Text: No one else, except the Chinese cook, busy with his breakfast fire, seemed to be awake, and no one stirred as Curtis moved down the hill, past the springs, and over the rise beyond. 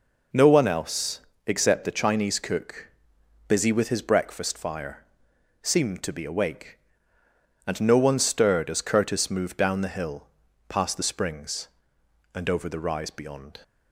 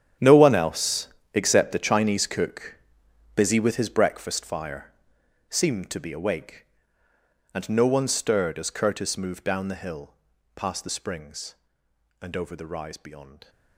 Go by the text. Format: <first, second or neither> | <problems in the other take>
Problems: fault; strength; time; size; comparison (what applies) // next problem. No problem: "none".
first | gets quieter; strong; throughout; 16.5 dB